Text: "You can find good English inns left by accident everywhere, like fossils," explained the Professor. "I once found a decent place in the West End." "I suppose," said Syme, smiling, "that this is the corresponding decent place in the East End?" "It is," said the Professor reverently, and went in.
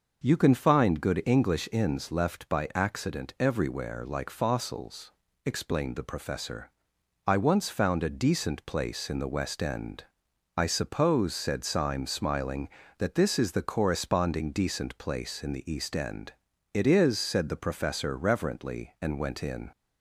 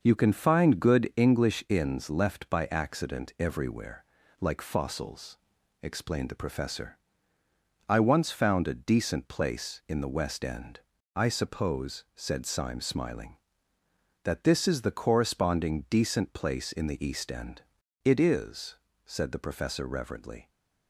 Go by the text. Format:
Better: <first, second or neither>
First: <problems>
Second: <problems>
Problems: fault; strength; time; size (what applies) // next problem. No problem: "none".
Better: first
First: none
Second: starts louder than the rest; noticeable; until 1.0 s; 6 dB // stops before "and went in"; at 20.4 s